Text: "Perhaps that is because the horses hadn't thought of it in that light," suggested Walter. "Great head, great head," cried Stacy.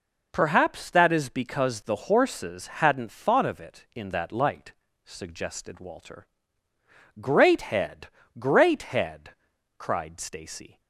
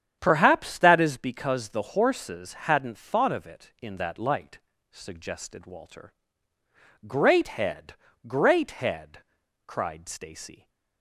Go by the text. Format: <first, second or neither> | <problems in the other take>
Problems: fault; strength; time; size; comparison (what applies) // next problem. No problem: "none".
first | starts louder than the rest; strong; until 1.2 s; 9 dB